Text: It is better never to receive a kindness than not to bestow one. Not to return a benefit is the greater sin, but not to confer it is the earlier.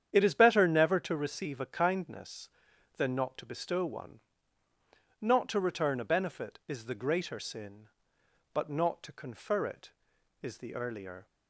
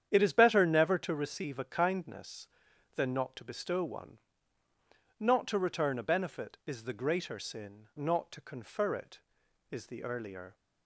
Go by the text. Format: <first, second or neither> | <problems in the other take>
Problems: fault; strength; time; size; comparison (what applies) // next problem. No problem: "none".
first | starts louder than the rest; strong; until 1.1 s; 9 dB; strong in the first // skips "but"; at 7.9 s